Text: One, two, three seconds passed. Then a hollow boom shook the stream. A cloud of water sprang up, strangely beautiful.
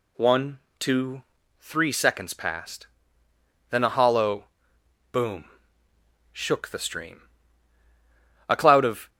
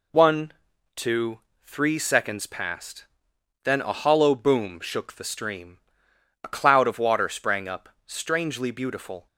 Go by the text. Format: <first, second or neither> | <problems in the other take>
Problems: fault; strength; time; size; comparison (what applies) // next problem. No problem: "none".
second | pauses between "hollow" and "boom"; noticeable; at 4.4 s; 0.66 s long // pauses between "boom" and "shook"; noticeable; at 5.4 s; 0.86 s long // stops before "water sprang up strangely beautiful"; at 9.0 s